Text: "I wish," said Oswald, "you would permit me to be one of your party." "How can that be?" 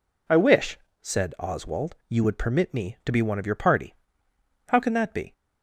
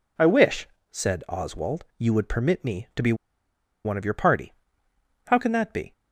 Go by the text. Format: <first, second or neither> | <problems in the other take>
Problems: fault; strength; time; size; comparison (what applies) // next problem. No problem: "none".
first | pauses between "be" and "one"; noticeable; at 3.1 s; 0.70 s long